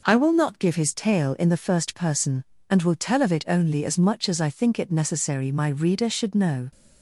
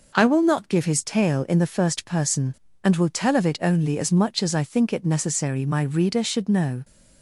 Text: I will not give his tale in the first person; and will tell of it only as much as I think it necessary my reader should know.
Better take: neither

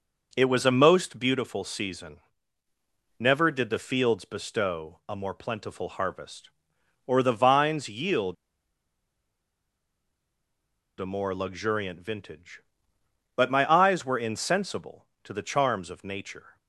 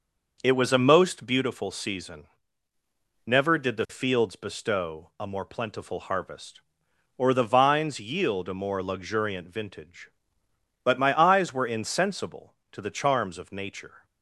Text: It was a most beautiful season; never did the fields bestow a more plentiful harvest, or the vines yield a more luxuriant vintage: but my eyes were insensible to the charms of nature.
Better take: second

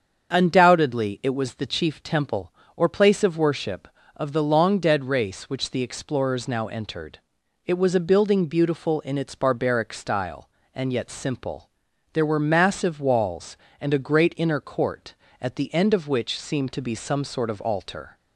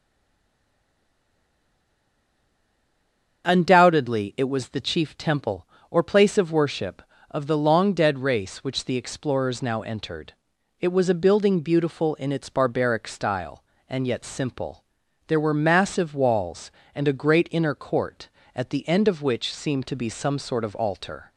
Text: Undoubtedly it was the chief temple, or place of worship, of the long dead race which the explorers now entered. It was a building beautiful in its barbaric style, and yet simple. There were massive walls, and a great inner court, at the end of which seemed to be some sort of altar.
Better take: first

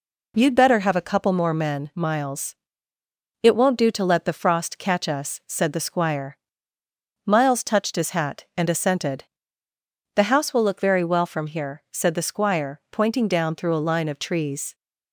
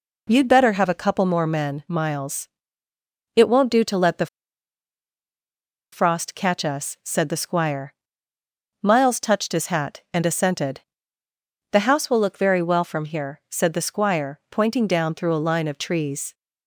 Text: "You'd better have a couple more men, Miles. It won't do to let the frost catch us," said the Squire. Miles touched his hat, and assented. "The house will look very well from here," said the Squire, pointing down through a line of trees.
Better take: first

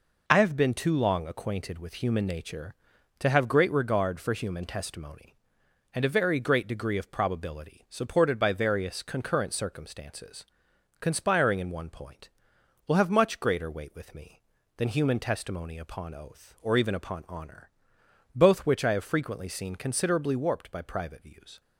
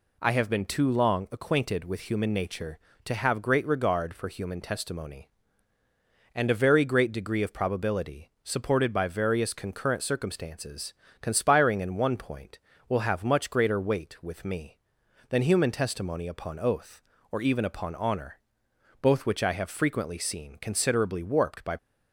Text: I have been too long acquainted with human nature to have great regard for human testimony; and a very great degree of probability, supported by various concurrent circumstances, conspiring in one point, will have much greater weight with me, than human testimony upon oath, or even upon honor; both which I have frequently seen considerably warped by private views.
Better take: first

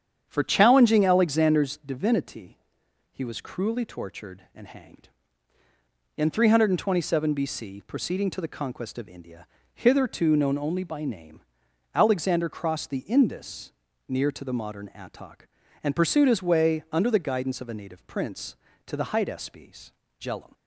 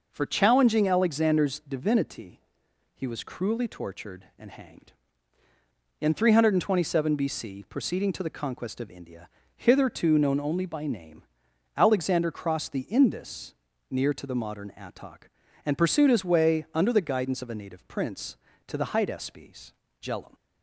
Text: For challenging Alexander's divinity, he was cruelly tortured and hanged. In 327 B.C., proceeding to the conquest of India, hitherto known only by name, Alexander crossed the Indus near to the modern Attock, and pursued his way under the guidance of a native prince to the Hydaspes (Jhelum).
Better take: second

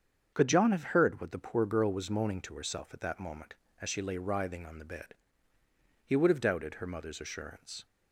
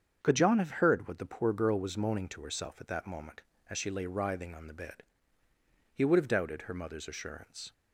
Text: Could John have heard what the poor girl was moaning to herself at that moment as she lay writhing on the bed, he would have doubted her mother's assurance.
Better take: neither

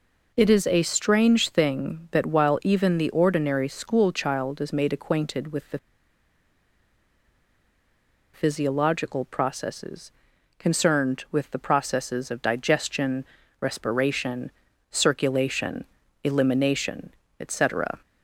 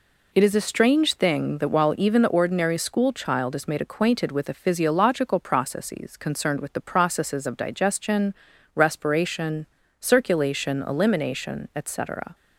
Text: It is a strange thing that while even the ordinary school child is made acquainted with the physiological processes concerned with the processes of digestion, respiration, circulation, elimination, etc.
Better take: second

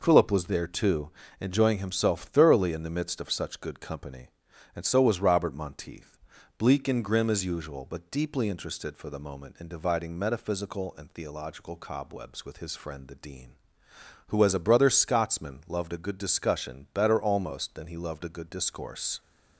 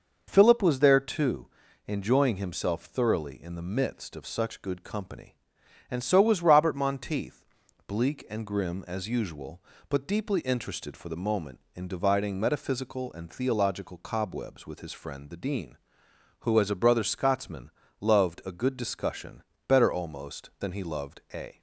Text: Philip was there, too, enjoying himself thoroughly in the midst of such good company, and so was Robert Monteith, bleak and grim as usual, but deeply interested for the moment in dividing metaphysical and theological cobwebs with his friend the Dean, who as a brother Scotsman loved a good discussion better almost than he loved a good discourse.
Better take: first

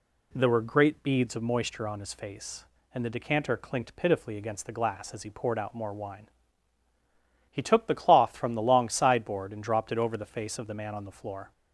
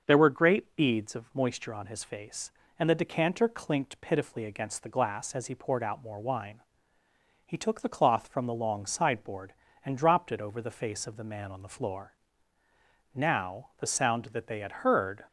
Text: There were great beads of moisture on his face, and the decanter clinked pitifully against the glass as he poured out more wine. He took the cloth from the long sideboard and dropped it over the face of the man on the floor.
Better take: first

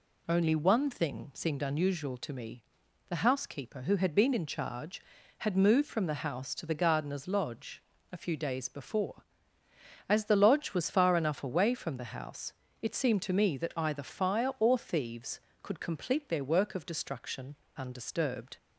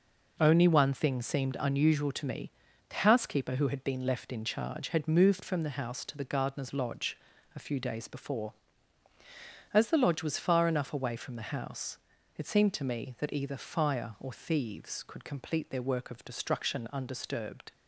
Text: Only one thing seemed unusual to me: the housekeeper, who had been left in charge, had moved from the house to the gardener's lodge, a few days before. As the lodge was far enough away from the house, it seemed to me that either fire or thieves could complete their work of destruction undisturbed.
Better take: second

